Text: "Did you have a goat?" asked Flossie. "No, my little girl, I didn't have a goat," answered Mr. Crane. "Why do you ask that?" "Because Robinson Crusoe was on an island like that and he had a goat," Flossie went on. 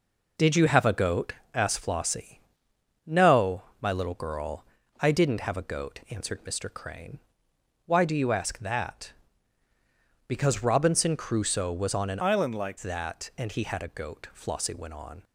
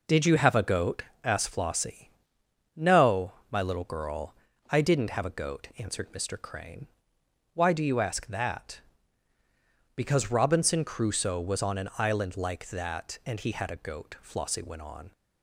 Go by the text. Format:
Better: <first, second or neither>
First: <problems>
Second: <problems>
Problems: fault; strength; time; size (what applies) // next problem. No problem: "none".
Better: second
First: changes voice from "island" to "like"; from 12.2 to 12.7 s; 0.5 s long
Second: none